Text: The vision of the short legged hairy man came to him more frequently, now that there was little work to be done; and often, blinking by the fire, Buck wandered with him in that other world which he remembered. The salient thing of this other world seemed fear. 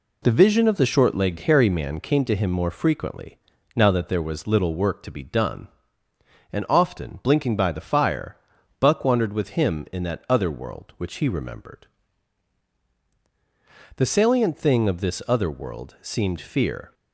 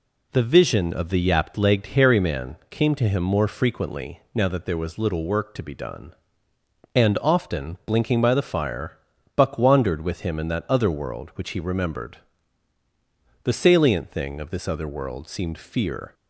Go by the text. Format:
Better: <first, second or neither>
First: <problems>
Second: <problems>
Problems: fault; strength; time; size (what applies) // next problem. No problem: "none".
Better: first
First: none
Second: says "yapped" for "short"; at 1.2 s